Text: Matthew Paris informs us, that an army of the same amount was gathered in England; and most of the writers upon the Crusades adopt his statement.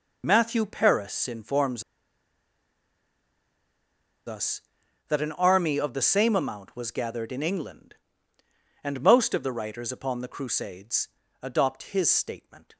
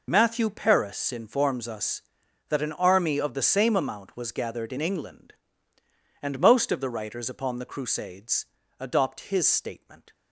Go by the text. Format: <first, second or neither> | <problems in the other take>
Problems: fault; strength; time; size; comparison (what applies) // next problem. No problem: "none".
second | pauses between "informs" and "us"; strong; at 1.8 s; 2.4 s long // pauses between "Crusades" and "adopt"; slight; at 11.0 s; 0.32 s long; slight in the second